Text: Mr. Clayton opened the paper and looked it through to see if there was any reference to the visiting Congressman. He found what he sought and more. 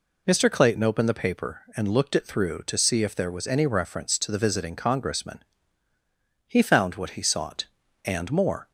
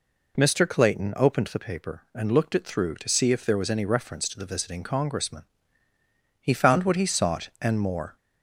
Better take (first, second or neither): neither